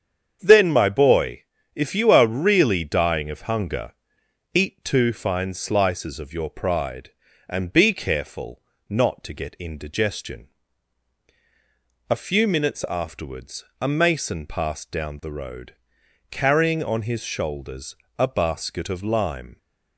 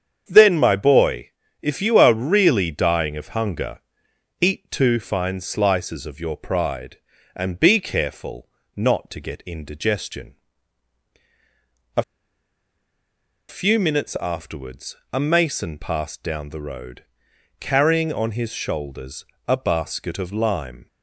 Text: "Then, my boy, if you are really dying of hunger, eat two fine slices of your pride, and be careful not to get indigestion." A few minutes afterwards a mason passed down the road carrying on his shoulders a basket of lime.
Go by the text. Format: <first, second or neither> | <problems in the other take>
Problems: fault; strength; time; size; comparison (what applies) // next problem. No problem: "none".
first | starts louder than the rest; strong; until 1.2 s; 7.5 dB; strong in the first // pauses between "careful" and "not"; slight; at 8.4 s; 0.28 s long; slight in the first // pauses between "A" and "few"; strong; at 12.0 s; 1.4 s long // pauses between "afterwards" and "a"; slight; at 14.9 s; 0.18 s long; slight in the first // pauses between "road" and "carrying"; noticeable; at 17.0 s; 0.56 s long; noticeable in the first // pauses between "shoulders" and "a"; slight; at 19.2 s; 0.22 s long; slight in the first